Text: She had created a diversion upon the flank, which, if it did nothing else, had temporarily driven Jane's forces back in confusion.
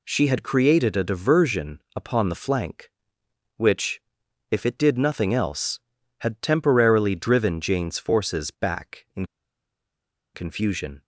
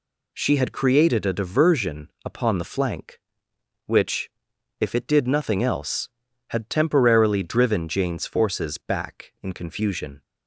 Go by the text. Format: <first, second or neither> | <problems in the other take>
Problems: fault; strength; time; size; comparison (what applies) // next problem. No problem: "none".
second | pauses between "in" and "confusion"; at 9.2 s; 1.0 s long